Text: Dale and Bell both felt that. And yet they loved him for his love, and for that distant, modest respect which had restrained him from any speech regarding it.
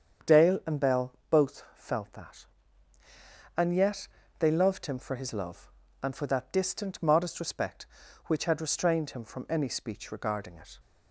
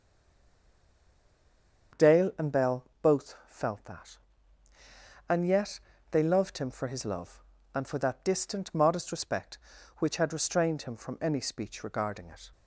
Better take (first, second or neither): first